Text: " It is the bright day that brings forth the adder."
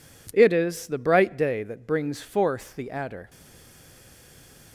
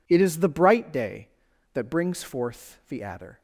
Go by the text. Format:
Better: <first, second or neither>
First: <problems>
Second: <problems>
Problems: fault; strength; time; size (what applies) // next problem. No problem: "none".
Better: second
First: stays silent after the last word; noticeable; from 3.2 s on; 1.5 s long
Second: none